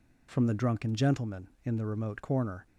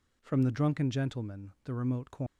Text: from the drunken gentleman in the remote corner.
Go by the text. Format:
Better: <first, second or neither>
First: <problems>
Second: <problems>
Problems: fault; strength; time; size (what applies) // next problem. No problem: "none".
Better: first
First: none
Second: skips "in"; at 1.5 s